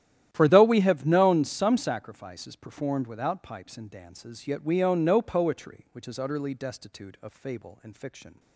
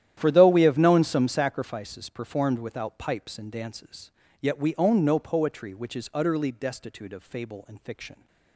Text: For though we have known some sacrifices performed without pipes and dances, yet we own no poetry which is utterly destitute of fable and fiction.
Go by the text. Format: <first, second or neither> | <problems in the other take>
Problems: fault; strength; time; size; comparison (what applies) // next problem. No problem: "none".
neither | starts louder than the rest; strong; the same in both